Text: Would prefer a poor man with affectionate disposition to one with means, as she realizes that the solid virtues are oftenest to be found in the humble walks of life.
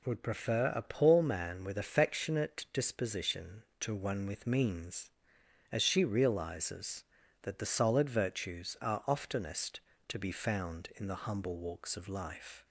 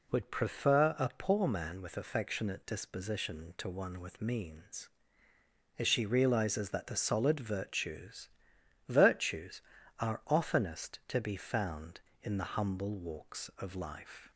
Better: first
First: none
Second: says "virtues" twice; at 8.8 s

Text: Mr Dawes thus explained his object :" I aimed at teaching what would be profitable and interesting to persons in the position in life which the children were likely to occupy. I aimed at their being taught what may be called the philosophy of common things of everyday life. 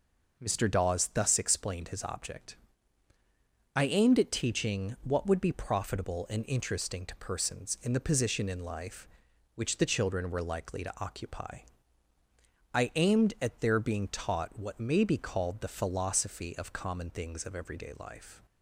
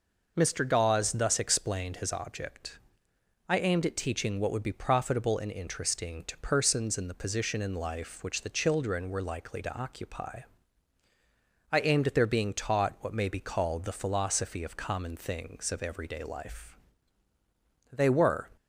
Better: first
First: none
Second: goes on to say "They were"; from 17.9 s on; 0.60 s long

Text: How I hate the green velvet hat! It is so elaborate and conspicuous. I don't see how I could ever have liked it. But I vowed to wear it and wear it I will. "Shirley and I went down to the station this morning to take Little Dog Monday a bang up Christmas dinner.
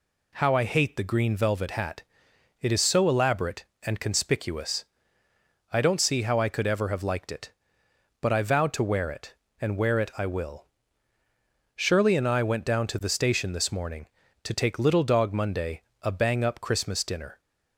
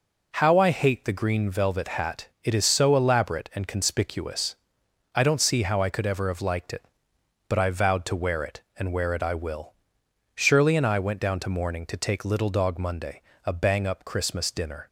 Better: first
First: pauses between "Monday" and "a"; slight; at 15.8 s; 0.18 s long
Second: skips "the station this"; at 11.4 s // pauses between "Monday" and "a"; slight; at 13.2 s; 0.22 s long

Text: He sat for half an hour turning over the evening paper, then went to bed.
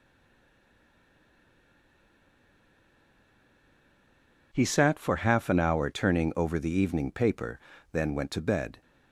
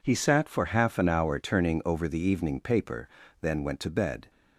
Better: second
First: stays silent before the first word; strong; until 4.5 s; 4.5 s long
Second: none

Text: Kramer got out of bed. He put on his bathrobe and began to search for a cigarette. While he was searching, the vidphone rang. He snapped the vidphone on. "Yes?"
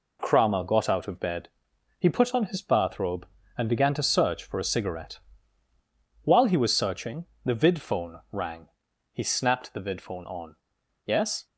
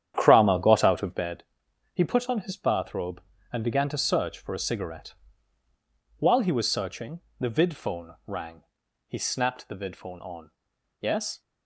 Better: first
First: none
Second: starts louder than the rest; strong; until 1.3 s; 9.5 dB

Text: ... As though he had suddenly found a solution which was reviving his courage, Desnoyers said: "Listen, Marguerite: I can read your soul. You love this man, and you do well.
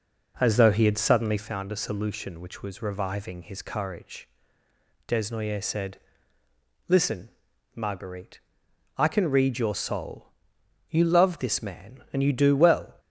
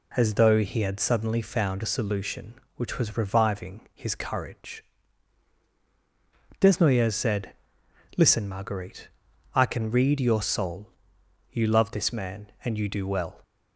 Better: second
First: starts louder than the rest; noticeable; until 1.6 s; 5 dB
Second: none

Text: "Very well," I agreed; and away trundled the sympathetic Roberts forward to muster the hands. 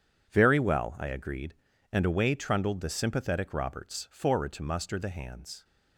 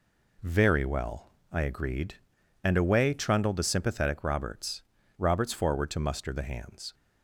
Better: first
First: none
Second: says "Roberts" twice; at 5.1 s

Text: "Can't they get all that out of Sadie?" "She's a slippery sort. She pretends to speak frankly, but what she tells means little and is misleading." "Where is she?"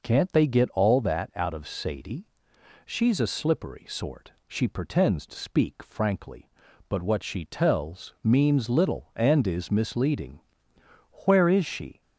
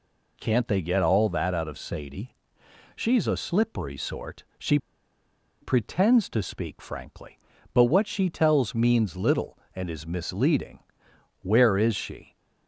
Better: first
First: none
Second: pauses between "She" and "pretends"; noticeable; at 4.7 s; 0.84 s long

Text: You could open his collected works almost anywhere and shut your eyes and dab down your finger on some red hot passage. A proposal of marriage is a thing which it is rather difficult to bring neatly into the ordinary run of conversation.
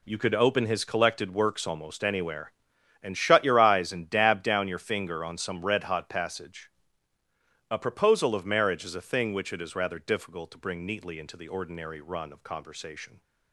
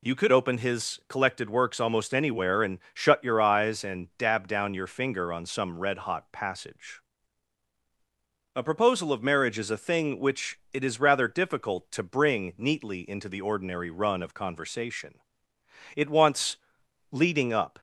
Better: first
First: none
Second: goes on to say "It wants leading up"; strong; from 15.9 s on; 1.8 s long

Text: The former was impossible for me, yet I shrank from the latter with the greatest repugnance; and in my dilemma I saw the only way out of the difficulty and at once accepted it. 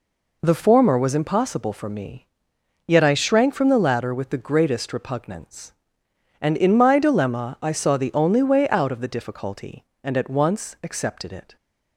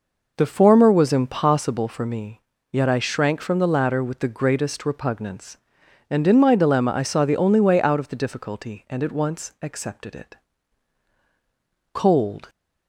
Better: first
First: none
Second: goes on to say "Cold"; from 11.9 s on; 0.56 s long

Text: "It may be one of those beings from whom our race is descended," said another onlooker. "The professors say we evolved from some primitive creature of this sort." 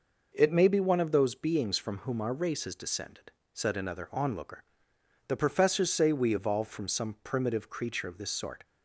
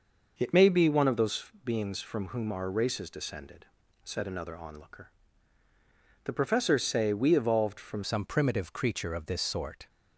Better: first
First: none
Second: pauses between "those" and "beings"; slight; at 1.4 s; 0.16 s long // changes voice at "some"; from 8.0 s on; 1.8 s long

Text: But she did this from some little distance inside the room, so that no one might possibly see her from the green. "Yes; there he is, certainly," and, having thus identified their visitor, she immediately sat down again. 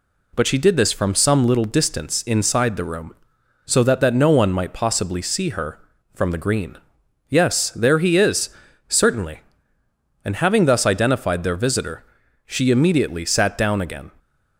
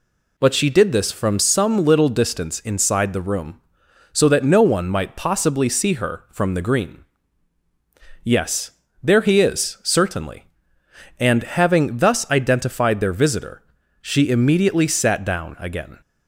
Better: second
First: says "that" twice; at 4.0 s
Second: none

